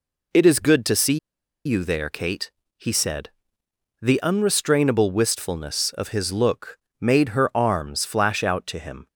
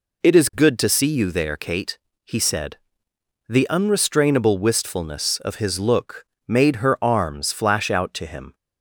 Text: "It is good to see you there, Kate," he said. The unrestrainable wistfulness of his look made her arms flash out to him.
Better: second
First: pauses between "see" and "you"; noticeable; at 1.1 s; 0.46 s long // pauses between "look" and "made"; slight; at 6.7 s; 0.24 s long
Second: pauses between "look" and "made"; slight; at 6.2 s; 0.24 s long

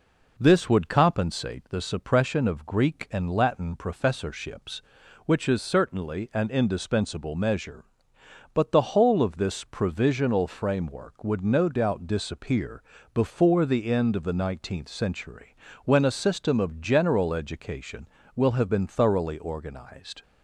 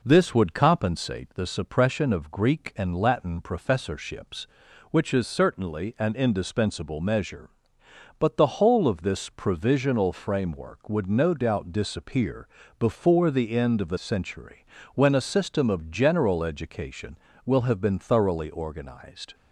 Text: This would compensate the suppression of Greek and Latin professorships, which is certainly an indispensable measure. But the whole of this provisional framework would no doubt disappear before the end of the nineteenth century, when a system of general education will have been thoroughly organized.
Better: first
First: pauses between "disappear" and "before"; slight; at 12.8 s; 0.30 s long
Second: pauses between "disappear" and "before"; slight; at 12.4 s; 0.30 s long // skips "nineteenth"; at 13.9 s

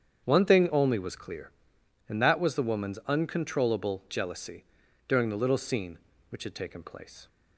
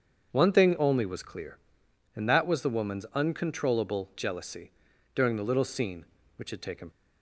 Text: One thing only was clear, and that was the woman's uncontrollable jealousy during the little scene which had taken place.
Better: first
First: starts louder than the rest; strong; until 1.2 s; 8 dB // pauses between "jealousy" and "during"; at 4.6 s; 0.42 s long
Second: starts louder than the rest; until 1.3 s; 7 dB // pauses between "jealousy" and "during"; at 4.7 s; 0.42 s long // stops before "place"; at 6.9 s

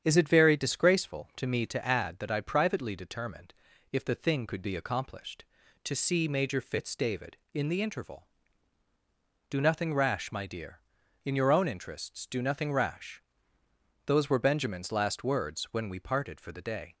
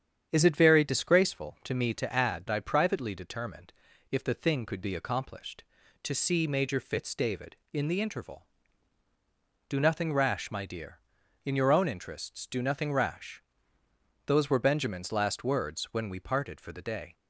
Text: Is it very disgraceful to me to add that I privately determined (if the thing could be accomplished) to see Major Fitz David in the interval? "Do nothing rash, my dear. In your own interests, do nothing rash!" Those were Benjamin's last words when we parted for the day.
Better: first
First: starts louder than the rest; strong; until 1.0 s; 8.5 dB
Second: starts louder than the rest; strong; until 1.3 s; 8.5 dB // skips "that"; at 2.4 s

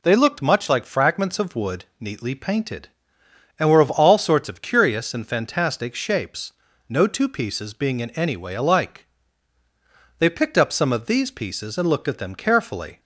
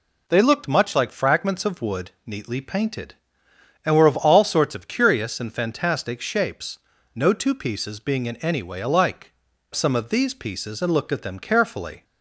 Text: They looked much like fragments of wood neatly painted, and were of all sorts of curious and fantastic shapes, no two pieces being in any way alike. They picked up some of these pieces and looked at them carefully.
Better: first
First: none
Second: skips "They picked up"; at 9.5 s

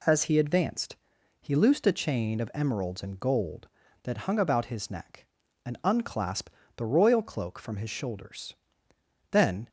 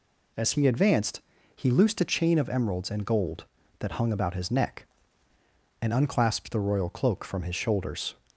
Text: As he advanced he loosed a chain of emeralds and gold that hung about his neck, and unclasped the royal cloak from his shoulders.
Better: second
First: pauses between "advanced" and "he"; at 0.9 s; 0.44 s long // pauses between "unclasped" and "the"; slight; at 6.5 s; 0.24 s long // goes on to say "Then"; slight; from 9.3 s on; 0.38 s long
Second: pauses between "advanced" and "he"; slight; at 1.2 s; 0.34 s long

